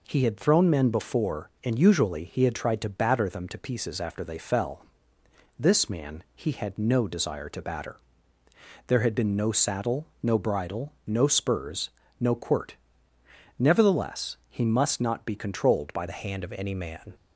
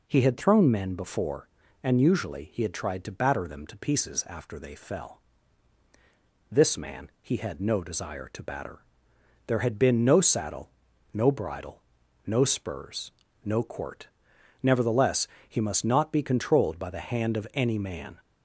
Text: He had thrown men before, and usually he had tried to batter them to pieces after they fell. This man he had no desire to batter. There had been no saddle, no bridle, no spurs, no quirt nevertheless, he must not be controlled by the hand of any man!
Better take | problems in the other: second | pauses between "quirt" and "nevertheless"; noticeable; at 12.7 s; 0.82 s long; noticeable in the second // changes voice at "the"; from 16.0 s on; 1.1 s long

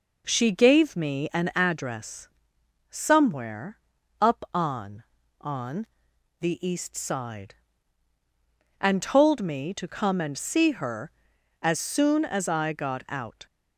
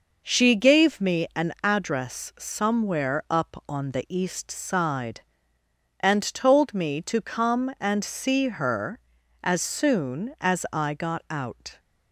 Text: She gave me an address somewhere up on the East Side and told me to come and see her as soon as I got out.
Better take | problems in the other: second | pauses between "address" and "somewhere"; noticeable; at 2.2 s; 0.62 s long // pauses between "somewhere" and "up"; at 3.7 s; 0.42 s long // says "on" twice; at 5.3 s

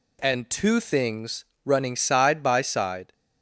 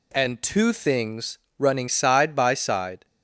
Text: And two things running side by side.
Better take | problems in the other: neither | pauses between "things" and "running"; slight; the same in both

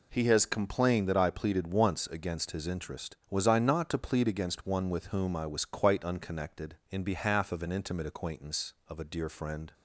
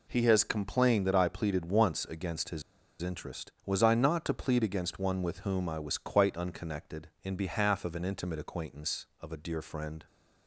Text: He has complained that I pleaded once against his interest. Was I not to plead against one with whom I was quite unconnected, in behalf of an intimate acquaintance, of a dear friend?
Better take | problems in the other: first | pauses between "his" and "interest"; at 2.6 s; 0.39 s long

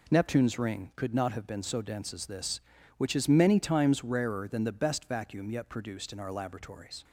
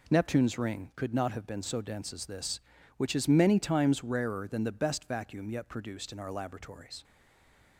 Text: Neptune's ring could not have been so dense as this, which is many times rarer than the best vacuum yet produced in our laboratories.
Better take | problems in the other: first | stays silent after the last word; slight; from 7.0 s on; 0.7 s long

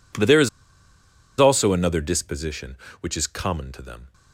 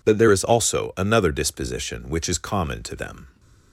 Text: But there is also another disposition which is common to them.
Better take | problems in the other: second | pauses between "is" and "also"; noticeable; at 0.4 s; 0.91 s long

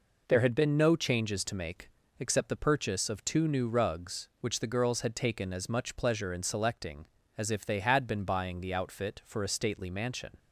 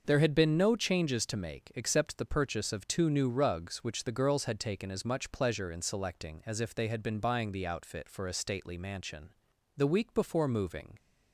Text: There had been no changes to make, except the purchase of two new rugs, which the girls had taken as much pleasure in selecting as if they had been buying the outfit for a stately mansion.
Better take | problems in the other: first | starts louder than the rest; noticeable; until 1.0 s; 6 dB // goes on to say "The week before moving"; noticeable; from 9.7 s on; 1.2 s long

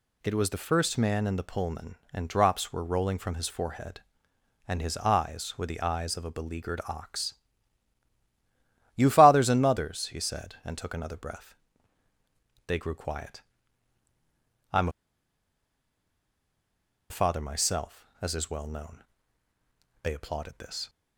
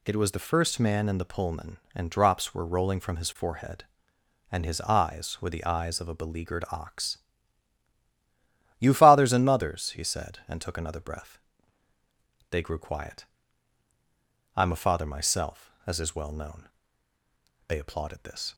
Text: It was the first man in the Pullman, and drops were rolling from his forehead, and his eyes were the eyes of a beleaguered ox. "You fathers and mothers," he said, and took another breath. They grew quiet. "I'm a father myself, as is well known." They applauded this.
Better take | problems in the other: second | pauses between "I'm" and "a"; strong; at 14.8 s; 2.2 s long

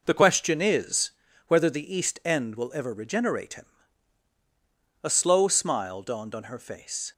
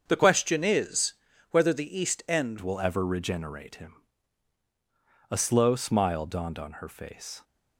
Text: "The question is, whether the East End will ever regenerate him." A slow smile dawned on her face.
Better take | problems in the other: first | starts louder than the rest; until 1.0 s; 7 dB // changes voice at "will"; from 2.5 s on; 4.9 s long

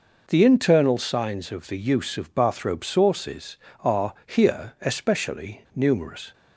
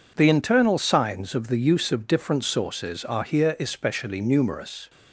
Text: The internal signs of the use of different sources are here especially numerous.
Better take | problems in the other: second | says "bathrobe" for "different"; at 2.3 s

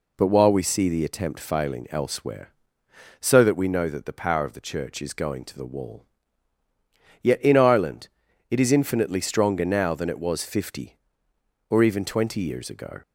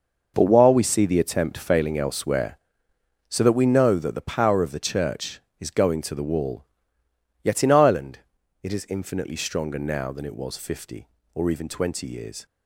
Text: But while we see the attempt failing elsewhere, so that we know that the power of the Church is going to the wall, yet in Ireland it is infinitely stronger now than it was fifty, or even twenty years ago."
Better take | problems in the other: first | pauses between "Ireland" and "it"; at 8.1 s; 0.42 s long; also in the first // stops before "ago"; at 12.4 s

